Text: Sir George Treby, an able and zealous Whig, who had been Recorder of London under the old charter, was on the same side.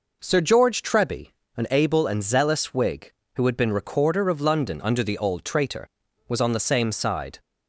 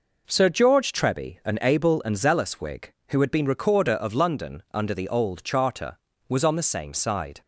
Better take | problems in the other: second | says "traitor" for "charter"; at 5.4 s

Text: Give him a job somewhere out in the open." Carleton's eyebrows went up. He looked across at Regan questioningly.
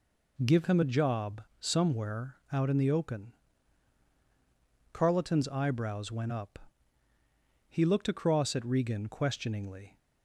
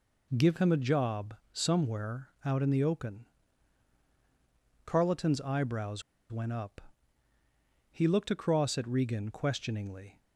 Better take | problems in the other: first | pauses between "job" and "somewhere"; slight; at 1.3 s; 0.18 s long; slight in the first // pauses between "somewhere" and "out"; slight; at 2.2 s; 0.16 s long; slight in the first // pauses between "eyebrows" and "went"; slight; at 6.0 s; 0.28 s long

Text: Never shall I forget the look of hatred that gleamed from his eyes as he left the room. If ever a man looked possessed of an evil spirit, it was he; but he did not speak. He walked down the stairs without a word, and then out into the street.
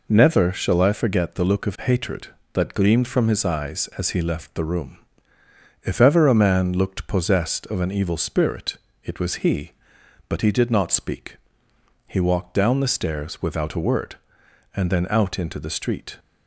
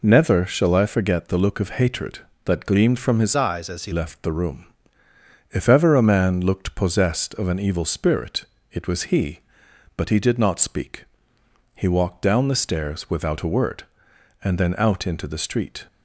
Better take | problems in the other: first | changes voice from "eyes" to "he"; from 3.3 to 3.9 s; 0.6 s long

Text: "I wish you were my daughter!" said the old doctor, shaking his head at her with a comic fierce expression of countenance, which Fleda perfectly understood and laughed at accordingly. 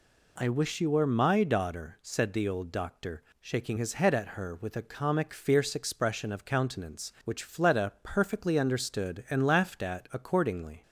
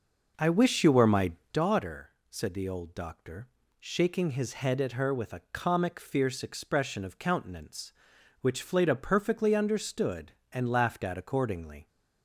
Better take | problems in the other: first | starts louder than the rest; noticeable; until 1.7 s; 5.5 dB // pauses between "my" and "daughter"; slight; at 1.3 s; 0.23 s long

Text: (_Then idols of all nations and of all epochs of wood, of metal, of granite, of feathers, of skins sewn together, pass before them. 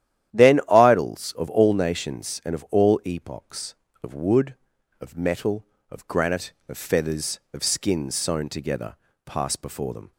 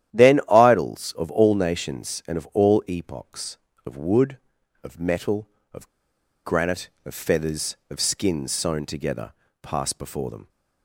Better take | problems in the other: first | starts louder than the rest; strong; until 1.2 s; 11.5 dB; strong in the first // pauses between "of" and "granite"; noticeable; at 5.8 s; 0.56 s long

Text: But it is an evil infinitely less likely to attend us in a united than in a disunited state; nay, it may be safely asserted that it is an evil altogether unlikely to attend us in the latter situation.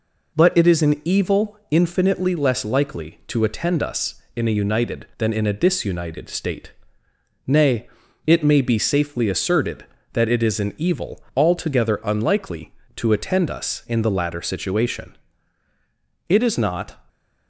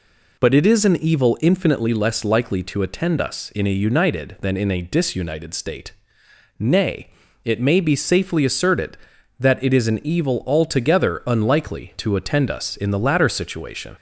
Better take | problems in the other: second | goes on to say "It is not"; noticeable; from 16.2 s on; 0.68 s long

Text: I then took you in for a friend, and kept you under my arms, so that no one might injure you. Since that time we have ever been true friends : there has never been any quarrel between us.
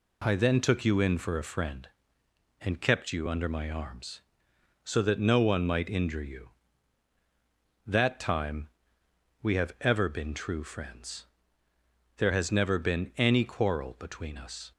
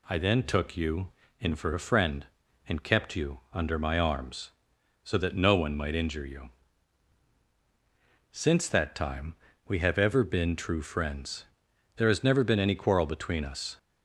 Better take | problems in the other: second | skips "Since"; at 7.1 s // pauses between "time" and "we"; noticeable; at 8.6 s; 0.72 s long; slight in the second

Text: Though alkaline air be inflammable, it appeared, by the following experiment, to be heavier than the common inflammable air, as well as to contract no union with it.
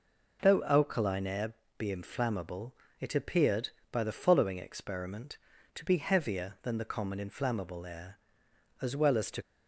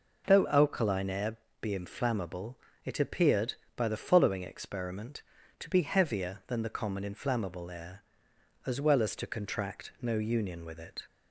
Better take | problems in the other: second | pauses between "air" and "be"; slight; at 1.5 s; 0.24 s long; slight in the second // stops before "contract no union with it"; at 9.4 s

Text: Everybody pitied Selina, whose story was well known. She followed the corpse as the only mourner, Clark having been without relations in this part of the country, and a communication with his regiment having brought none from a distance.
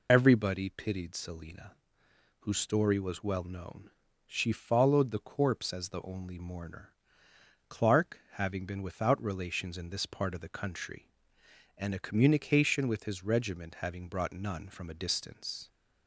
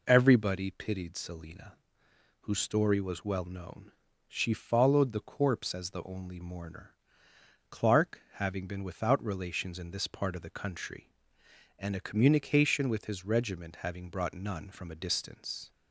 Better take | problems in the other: second | loses the start of "Everybody"; at 0.0 s; 45 ms

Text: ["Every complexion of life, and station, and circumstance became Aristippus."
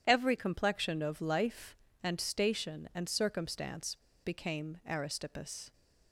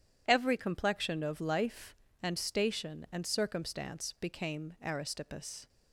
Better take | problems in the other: second | pauses between "circumstance" and "became"; slight; at 3.9 s; 0.27 s long

